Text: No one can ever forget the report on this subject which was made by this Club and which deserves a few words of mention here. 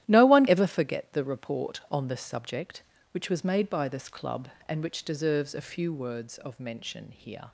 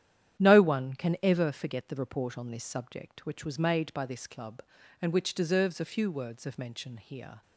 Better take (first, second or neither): second